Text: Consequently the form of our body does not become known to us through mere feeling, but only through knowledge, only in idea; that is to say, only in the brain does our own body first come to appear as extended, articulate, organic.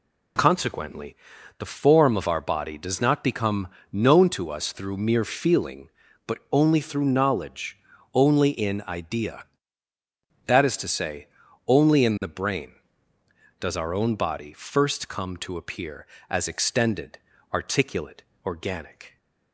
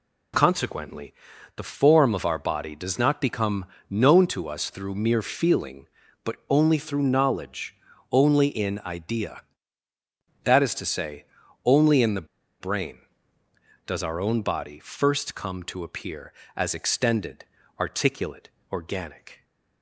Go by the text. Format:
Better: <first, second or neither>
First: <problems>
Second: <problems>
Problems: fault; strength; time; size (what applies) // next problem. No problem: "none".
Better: first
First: pauses between "Consequently" and "the"; at 1.1 s; 0.42 s long // pauses between "become" and "known"; slight; at 3.6 s; 0.24 s long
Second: pauses between "Consequently" and "the"; at 1.1 s; 0.42 s long // pauses between "become" and "known"; slight; at 3.6 s; 0.24 s long // pauses between "the" and "brain"; slight; at 12.2 s; 0.34 s long